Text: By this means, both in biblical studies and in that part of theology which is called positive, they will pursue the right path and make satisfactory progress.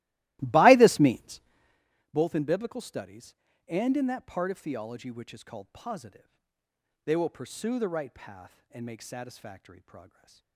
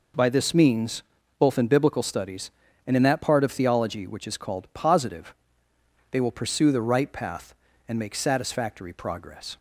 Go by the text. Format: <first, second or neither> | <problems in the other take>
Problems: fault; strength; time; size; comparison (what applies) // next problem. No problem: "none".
second | starts louder than the rest; strong; until 1.9 s; 18 dB // stays silent after the last word; slight; from 10.0 s on; 0.5 s long